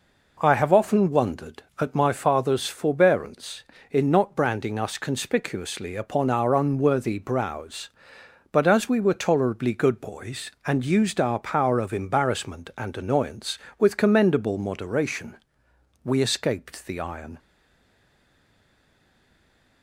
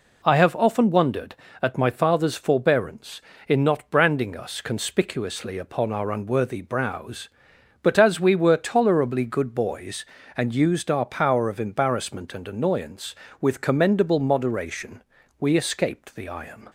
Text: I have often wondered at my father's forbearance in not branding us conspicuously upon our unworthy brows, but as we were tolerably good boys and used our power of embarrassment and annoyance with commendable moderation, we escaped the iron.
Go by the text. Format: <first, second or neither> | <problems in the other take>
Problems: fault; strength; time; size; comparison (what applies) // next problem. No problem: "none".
second | stays silent after the last word; from 17.3 s on; 2.5 s long